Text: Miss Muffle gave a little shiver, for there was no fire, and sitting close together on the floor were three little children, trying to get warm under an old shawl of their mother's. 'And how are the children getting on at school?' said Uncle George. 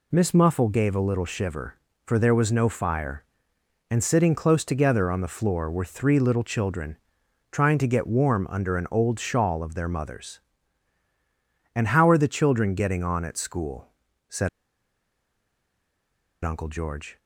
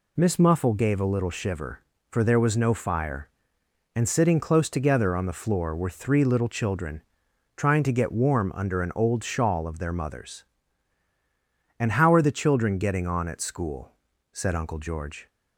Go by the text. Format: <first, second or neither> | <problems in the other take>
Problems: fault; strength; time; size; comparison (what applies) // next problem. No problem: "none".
second | pauses between "said" and "Uncle"; strong; at 14.4 s; 1.9 s long